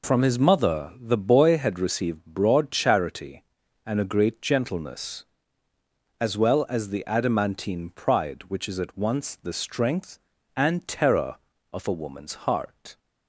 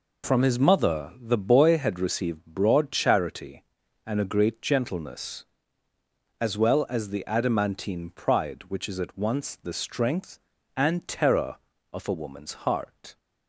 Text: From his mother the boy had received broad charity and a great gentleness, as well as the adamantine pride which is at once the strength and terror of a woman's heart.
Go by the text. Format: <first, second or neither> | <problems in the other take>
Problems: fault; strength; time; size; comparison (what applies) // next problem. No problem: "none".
neither | none